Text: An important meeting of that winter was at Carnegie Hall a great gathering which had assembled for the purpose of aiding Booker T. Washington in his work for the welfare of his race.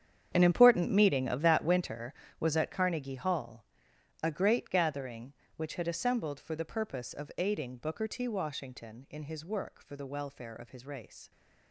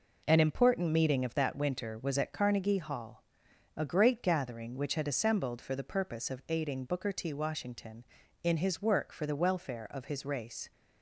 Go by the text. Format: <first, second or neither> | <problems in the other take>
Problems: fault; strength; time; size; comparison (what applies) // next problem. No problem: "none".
second | gets quieter; strong; throughout; 15.5 dB // pauses between "Hall" and "a"; noticeable; at 3.6 s; 0.58 s long; noticeable in the second